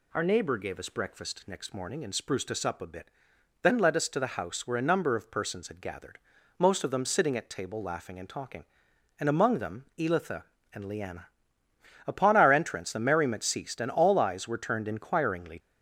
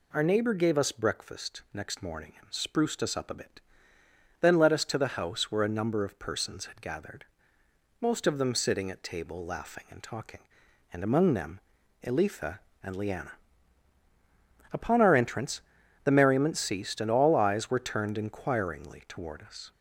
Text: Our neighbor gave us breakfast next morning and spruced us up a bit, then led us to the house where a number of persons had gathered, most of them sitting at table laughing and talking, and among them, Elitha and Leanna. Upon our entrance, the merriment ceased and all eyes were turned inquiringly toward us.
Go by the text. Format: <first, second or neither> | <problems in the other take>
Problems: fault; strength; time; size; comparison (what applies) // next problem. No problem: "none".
second | stops before "toward us"; at 15.5 s